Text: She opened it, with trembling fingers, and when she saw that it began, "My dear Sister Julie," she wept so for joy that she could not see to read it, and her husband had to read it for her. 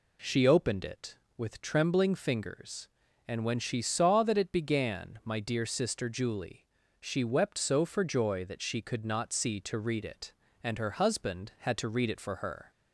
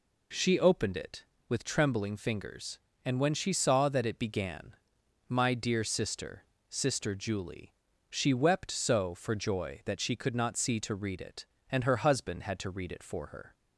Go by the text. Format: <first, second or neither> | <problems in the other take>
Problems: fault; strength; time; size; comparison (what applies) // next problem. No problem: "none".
first | says "Sister" twice; at 6.6 s